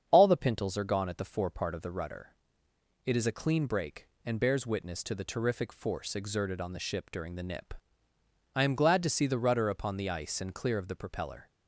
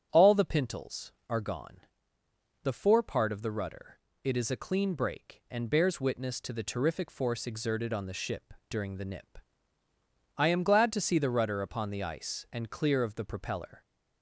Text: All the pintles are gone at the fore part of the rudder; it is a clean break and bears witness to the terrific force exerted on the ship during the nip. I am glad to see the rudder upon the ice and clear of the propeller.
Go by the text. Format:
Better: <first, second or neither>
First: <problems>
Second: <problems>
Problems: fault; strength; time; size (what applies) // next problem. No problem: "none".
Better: first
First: starts louder than the rest; strong; until 1.1 s; 7.5 dB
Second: starts louder than the rest; strong; until 1.1 s; 8.5 dB // skips "at"; at 2.2 s // pauses between "ship" and "during"; slight; at 8.5 s; 0.18 s long